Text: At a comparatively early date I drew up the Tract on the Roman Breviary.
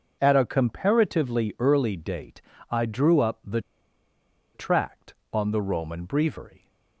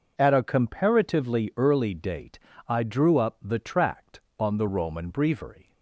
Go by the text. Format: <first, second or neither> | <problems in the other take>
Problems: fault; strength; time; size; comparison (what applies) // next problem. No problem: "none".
second | pauses between "date" and "I"; slight; at 2.4 s; 0.30 s long; slight in the second // pauses between "the" and "Tract"; noticeable; at 3.6 s; 0.93 s long